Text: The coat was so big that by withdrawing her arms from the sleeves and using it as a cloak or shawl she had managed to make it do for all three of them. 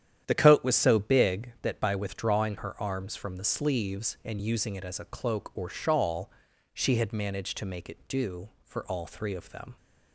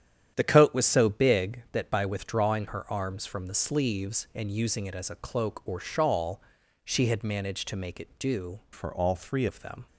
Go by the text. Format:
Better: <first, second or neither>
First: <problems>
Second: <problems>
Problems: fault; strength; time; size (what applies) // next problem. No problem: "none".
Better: first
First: starts louder than the rest; strong; until 1.2 s; 10 dB // pauses between "shawl" and "she"; at 6.3 s; 0.42 s long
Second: starts louder than the rest; strong; until 1.3 s; 9.5 dB // pauses between "shawl" and "she"; at 6.4 s; 0.42 s long // changes voice from "for" to "three"; from 8.7 to 9.4 s; 0.7 s long